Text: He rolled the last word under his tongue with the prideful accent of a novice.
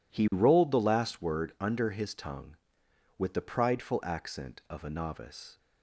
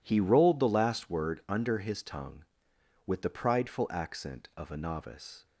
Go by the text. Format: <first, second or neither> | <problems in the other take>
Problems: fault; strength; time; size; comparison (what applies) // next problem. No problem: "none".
neither | none